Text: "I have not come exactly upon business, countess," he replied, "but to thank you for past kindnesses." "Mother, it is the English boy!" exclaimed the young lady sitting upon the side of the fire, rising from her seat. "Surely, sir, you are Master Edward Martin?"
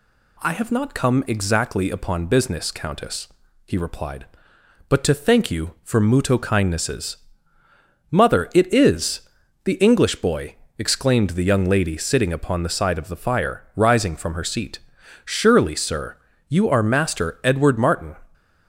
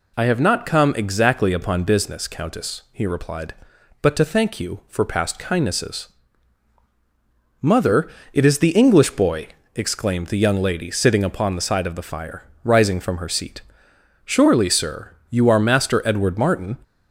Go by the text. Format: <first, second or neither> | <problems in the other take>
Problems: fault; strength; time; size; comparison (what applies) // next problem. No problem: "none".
second | says "muto" for "past"; at 5.9 s // pauses between "is" and "the"; at 9.2 s; 0.42 s long